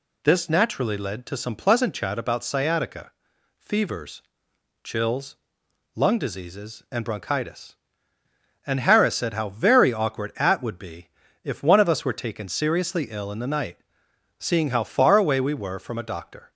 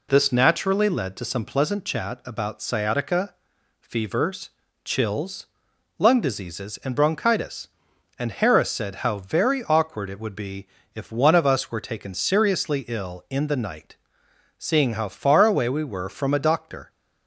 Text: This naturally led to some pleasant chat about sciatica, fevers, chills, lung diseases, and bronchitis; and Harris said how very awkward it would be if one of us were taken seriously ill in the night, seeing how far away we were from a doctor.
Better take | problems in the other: second | says "at" for "it"; at 10.3 s // pauses between "be" and "if"; slight; at 11.0 s; 0.36 s long; slight in the second

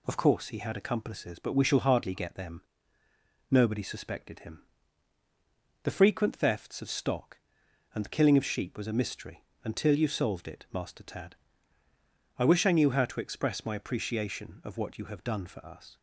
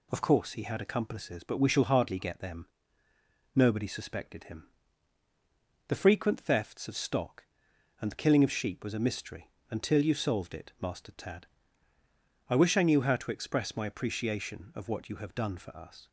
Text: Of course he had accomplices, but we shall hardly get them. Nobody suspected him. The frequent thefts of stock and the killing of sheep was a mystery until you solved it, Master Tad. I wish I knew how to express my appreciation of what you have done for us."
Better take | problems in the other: neither | pauses between "mystery" and "until"; slight; the same in both

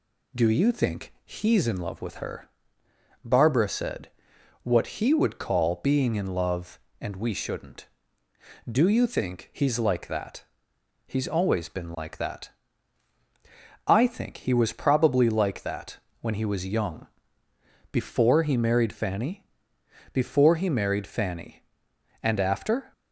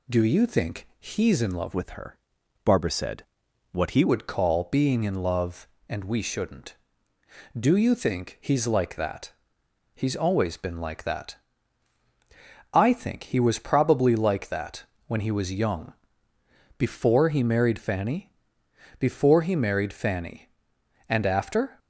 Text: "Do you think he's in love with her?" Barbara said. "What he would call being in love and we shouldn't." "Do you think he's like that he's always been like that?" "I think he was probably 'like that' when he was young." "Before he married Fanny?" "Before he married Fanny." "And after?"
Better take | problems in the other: first | changes voice from "with" to "he"; from 1.7 to 4.0 s; 2.3 s long // pauses between "that" and "he's"; noticeable; at 9.3 s; 0.62 s long; noticeable in the first // pauses between "that" and "when"; slight; at 14.8 s; 0.24 s long; slight in the first

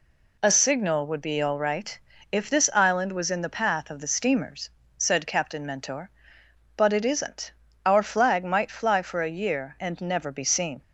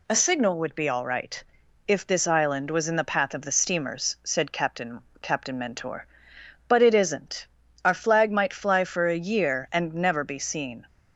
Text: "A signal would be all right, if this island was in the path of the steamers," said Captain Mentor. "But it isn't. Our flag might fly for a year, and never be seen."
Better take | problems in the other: first | says "Captain" twice; at 5.2 s

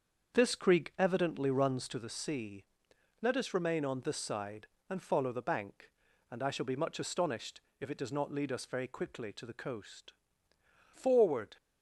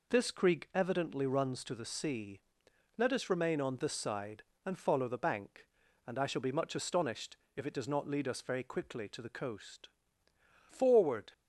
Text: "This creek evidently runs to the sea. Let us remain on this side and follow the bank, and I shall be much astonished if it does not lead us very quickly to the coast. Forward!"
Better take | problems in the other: second | starts louder than the rest; until 2.1 s; 7 dB // pauses between "astonished" and "if"; slight; at 7.6 s; 0.20 s long; slight in the second

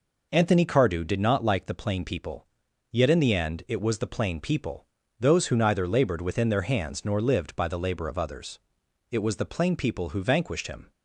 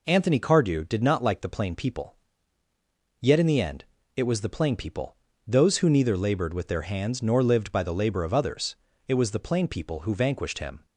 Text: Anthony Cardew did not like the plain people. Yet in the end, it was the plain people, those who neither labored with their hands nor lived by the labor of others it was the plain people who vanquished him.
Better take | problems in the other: second | says "within" for "with"; at 6.2 s // pauses between "others" and "it"; noticeable; at 8.5 s; 0.52 s long; slight in the second

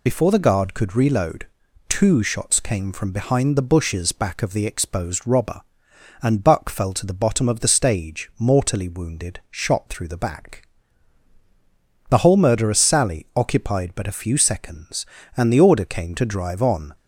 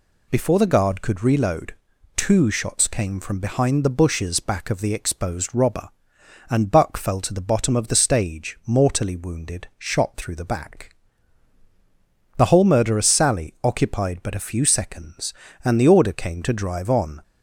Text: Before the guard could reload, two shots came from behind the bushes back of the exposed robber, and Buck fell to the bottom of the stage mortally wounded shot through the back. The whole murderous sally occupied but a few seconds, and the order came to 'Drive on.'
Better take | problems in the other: second | loses the start of "Before"; at 0.0 s; 35 ms

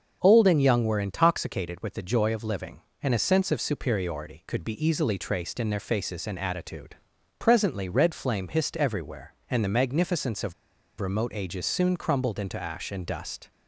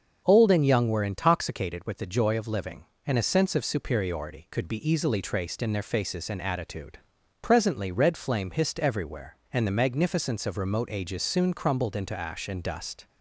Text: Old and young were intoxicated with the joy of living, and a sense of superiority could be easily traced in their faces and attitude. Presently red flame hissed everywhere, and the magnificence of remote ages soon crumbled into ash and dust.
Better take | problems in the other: second | starts louder than the rest; until 1.2 s; 6.5 dB; also in the second // pauses between "of" and "remote"; noticeable; at 10.5 s; 0.47 s long

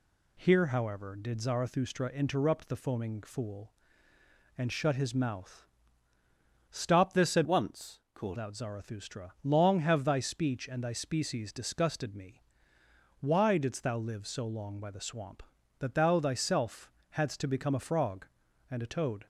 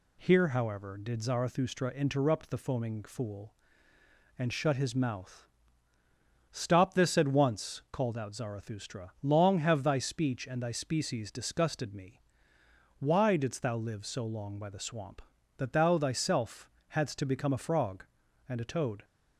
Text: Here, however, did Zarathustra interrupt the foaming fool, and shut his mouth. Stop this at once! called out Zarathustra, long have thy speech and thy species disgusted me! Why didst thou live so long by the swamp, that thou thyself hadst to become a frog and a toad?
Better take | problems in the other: second | changes voice from "once" to "called"; from 7.4 to 8.3 s; 0.9 s long // pauses between "thyself" and "hadst"; slight; at 16.8 s; 0.20 s long; slight in the second

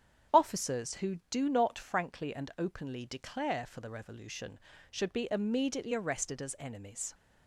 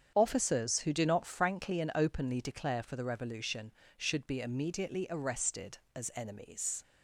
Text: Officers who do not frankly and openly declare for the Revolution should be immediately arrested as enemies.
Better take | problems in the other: neither | starts louder than the rest; strong; the same in both

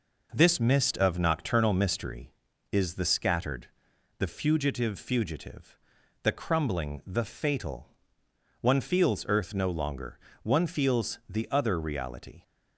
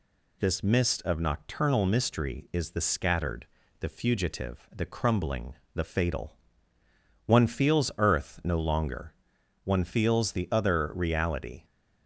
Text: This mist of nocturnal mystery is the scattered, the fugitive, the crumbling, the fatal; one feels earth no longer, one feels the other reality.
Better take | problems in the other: second | says "fugitive" twice; at 4.9 s

